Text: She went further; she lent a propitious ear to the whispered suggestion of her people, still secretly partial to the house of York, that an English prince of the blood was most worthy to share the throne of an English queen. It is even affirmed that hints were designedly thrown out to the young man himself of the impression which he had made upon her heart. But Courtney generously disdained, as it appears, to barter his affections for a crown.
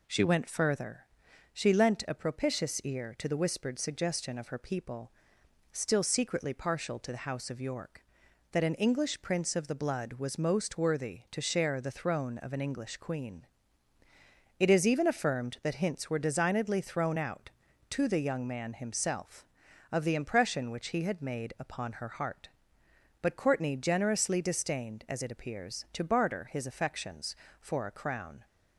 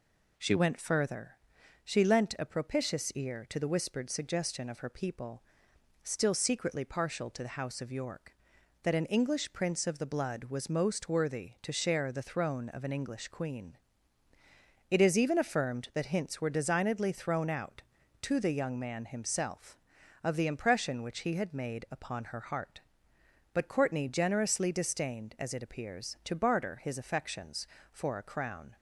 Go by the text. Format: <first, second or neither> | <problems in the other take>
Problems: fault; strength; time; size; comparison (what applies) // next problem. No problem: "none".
neither | none